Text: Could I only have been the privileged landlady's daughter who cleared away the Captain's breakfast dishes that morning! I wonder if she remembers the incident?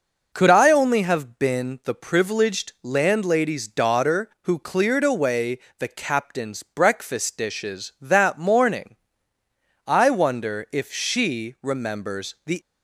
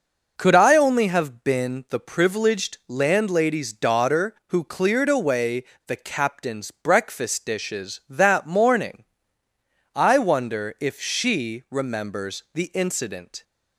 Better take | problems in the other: second | pauses between "away" and "the"; slight; at 5.5 s; 0.20 s long; slight in the second // stops before "incident"; at 12.6 s

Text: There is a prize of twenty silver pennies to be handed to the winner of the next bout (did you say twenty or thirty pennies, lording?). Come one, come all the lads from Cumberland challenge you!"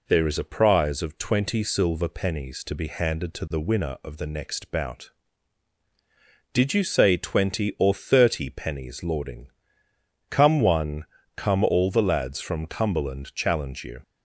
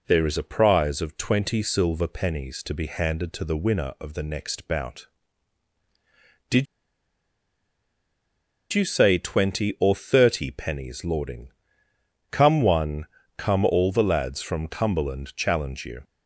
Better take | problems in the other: first | pauses between "did" and "you"; strong; at 6.6 s; 2.0 s long

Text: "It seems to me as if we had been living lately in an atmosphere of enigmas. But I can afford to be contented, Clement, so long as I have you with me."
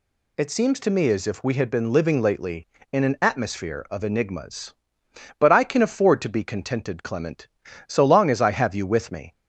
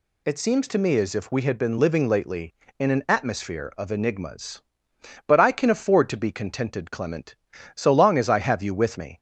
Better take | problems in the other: neither | none

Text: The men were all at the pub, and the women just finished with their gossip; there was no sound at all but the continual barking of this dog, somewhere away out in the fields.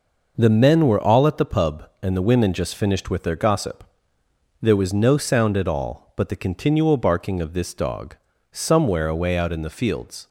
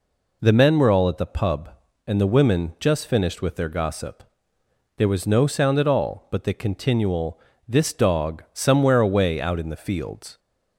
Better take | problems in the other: first | skips "barking of"; at 7.5 s

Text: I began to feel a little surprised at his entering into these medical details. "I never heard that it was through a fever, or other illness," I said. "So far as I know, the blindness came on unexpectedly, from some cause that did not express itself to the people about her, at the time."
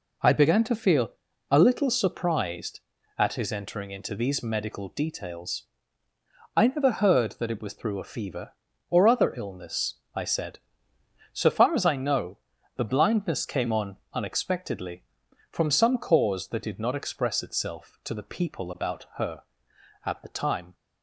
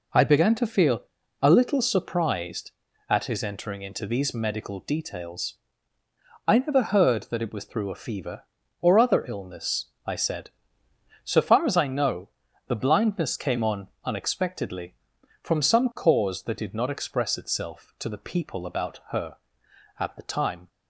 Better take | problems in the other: neither | pauses between "feel" and "a"; the same in both

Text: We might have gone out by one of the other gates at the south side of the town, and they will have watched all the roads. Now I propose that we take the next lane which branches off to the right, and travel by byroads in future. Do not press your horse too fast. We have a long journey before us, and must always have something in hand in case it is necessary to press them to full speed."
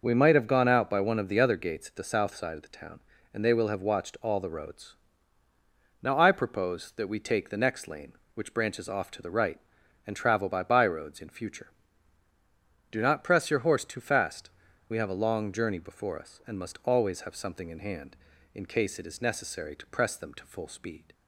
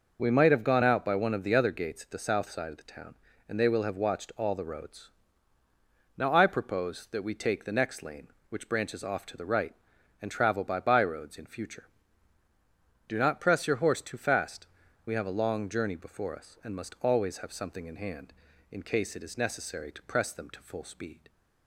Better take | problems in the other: neither | none

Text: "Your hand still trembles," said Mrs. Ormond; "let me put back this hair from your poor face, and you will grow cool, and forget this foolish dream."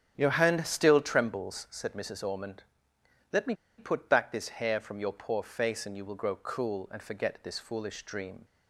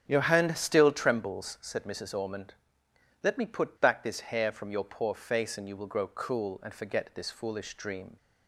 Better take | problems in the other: second | starts louder than the rest; strong; until 1.1 s; 8.5 dB; strong in the second // pauses between "me" and "put"; slight; at 3.5 s; 0.23 s long

